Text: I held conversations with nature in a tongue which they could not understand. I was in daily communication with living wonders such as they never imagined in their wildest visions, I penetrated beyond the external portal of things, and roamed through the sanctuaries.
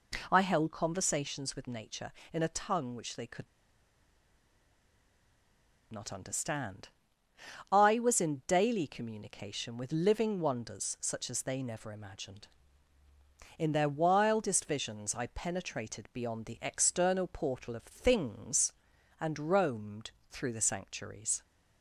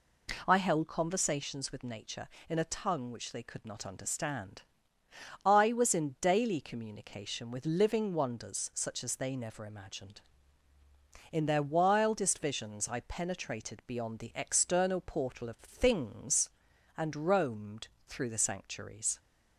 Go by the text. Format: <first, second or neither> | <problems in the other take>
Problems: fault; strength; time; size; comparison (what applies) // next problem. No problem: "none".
second | pauses between "could" and "not"; strong; at 3.4 s; 2.4 s long // pauses between "roamed" and "through"; slight; at 20.0 s; 0.20 s long; slight in the second